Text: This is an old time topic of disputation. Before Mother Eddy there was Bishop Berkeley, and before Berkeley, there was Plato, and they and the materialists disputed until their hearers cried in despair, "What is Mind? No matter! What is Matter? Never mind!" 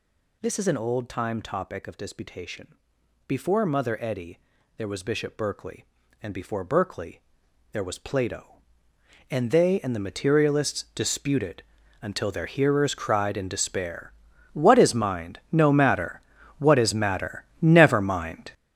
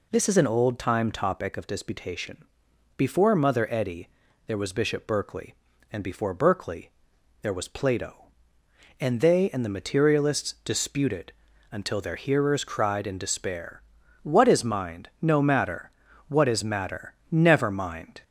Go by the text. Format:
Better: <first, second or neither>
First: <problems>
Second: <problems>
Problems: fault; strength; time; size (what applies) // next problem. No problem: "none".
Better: second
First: gets louder; strong; throughout; 10 dB // pauses between "Eddy" and "there"; at 4.3 s; 0.38 s long // pauses between "disputed" and "until"; at 11.6 s; 0.40 s long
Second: pauses between "Eddy" and "there"; at 4.0 s; 0.38 s long // pauses between "disputed" and "until"; at 11.3 s; 0.40 s long